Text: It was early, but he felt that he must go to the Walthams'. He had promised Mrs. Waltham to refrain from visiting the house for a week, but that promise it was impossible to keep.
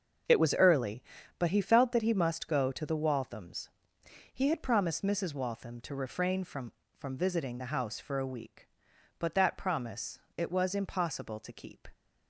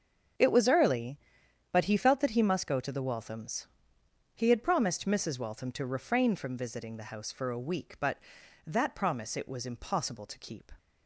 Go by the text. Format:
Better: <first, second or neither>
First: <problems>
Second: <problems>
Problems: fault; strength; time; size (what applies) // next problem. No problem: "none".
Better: second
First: starts louder than the rest; until 1.6 s; 6.5 dB // says "from" twice; at 6.9 s // pauses between "promise" and "it"; slight; at 10.1 s; 0.20 s long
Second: starts louder than the rest; until 1.9 s; 7 dB